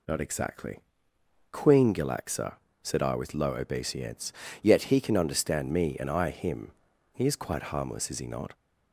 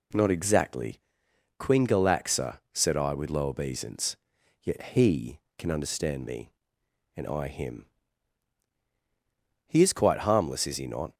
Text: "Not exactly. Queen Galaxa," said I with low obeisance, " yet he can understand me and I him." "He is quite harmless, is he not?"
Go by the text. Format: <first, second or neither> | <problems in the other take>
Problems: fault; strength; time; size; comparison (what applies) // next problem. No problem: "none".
neither | none